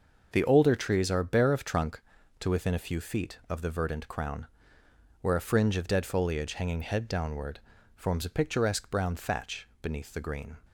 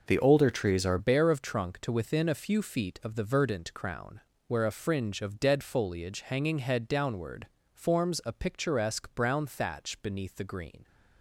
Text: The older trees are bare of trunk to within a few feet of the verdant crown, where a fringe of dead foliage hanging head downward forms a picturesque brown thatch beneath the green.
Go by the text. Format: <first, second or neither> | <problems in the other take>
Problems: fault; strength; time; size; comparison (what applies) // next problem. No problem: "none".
first | changes voice at "bare"; from 0.9 s on; 9.9 s long // pauses between "downward" and "forms"; slight; at 7.4 s; 0.24 s long; slight in the first